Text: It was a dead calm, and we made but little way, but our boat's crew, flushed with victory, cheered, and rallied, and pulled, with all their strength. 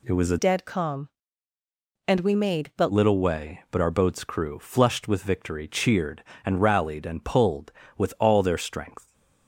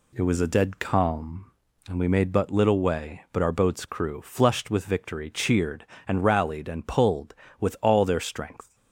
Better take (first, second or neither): second